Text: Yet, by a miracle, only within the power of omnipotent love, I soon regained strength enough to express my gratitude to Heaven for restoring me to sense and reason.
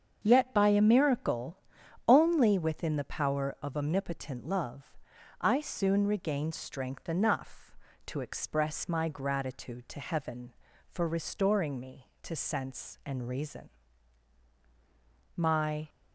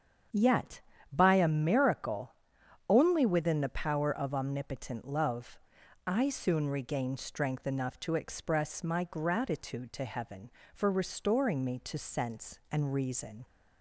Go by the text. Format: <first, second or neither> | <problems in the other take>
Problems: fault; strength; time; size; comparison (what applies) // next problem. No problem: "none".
second | starts louder than the rest; strong; until 1.2 s; 7 dB; strong in the second // goes on to say "My"; from 15.3 s on; 0.54 s long